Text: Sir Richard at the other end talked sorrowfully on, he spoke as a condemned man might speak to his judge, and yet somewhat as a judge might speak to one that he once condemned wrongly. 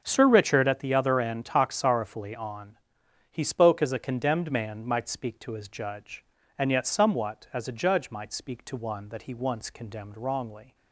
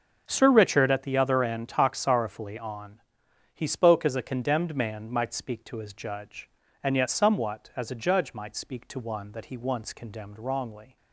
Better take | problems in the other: neither | none

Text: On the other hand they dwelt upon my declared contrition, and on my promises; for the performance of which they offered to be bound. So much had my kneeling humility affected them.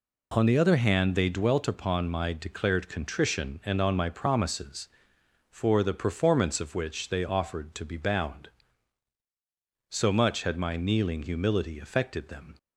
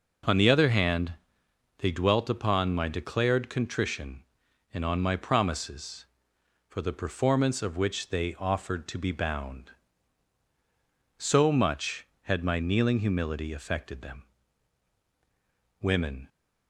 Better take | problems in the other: first | pauses between "hand" and "they"; noticeable; at 1.1 s; 0.64 s long // goes on to say "Women"; slight; from 15.8 s on; 0.46 s long

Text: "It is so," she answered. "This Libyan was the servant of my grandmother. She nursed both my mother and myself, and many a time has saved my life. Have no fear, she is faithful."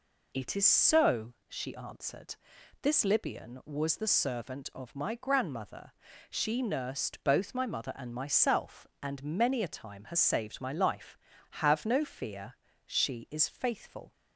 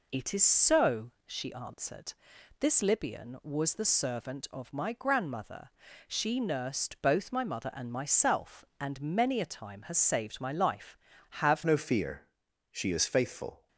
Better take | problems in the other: first | changes voice at "no"; from 11.6 s on; 2.0 s long

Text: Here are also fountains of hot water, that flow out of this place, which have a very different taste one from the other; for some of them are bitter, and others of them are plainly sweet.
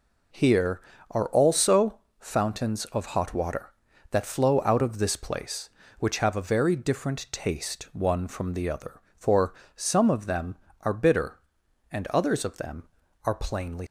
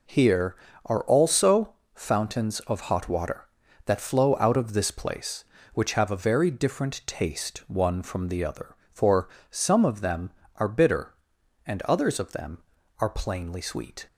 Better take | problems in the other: second | pauses between "also" and "fountains"; slight; at 1.9 s; 0.20 s long; slight in the second // pauses between "for" and "some"; slight; at 9.5 s; 0.24 s long; slight in the second // stops before "sweet"; at 13.8 s

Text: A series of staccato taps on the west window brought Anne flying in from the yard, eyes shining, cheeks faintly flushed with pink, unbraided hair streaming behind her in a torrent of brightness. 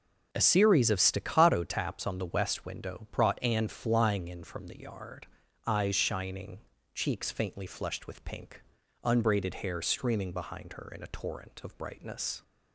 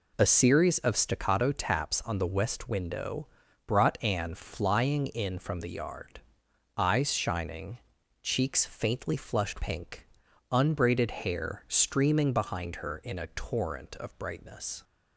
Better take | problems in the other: first | pauses between "window" and "brought"; at 3.2 s; 0.40 s long // skips "with"; at 9.6 s

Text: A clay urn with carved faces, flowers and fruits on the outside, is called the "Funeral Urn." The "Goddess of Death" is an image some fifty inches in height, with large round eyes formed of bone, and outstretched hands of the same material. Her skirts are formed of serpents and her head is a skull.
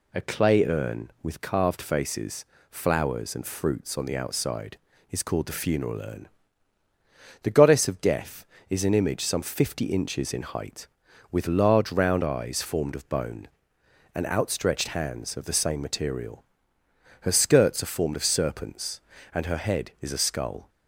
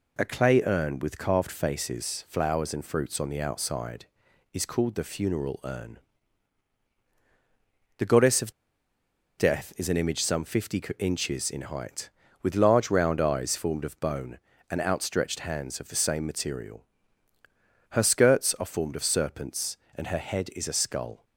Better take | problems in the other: first | pauses between "of" and "Death"; noticeable; at 8.5 s; 0.86 s long // pauses between "fifty" and "inches"; slight; at 10.7 s; 0.20 s long

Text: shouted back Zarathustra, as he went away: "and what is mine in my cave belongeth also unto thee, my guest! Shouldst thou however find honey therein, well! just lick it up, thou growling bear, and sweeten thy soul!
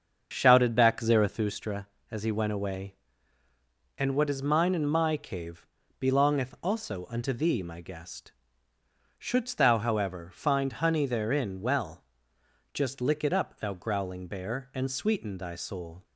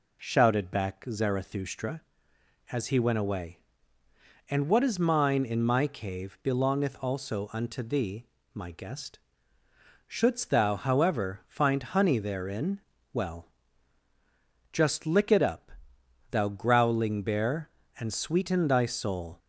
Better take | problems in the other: second | starts louder than the rest; until 1.4 s; 6.5 dB // pauses between "cave" and "belongeth"; slight; at 5.6 s; 0.34 s long

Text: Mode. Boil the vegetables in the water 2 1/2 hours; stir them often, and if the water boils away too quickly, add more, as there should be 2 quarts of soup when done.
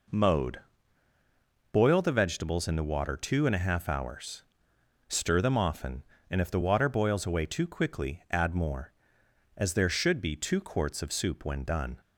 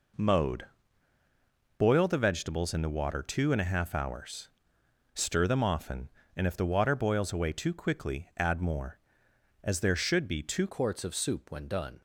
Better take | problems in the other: first | changes voice at "quarts"; from 10.6 s on; 1.4 s long

